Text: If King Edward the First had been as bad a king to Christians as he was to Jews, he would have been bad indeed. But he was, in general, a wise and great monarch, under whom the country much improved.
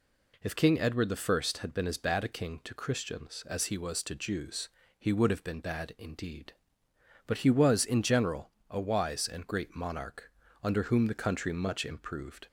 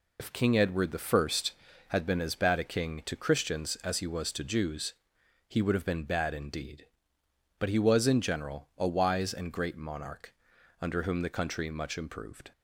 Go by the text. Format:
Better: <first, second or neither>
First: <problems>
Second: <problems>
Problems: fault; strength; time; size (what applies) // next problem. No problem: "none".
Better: first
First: none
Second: loses the start of "If"; at 0.1 s; 30 ms